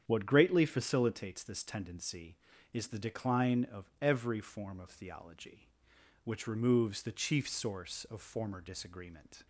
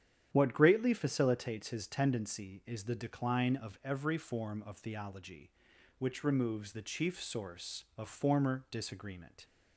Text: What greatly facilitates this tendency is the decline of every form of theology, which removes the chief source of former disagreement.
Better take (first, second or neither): first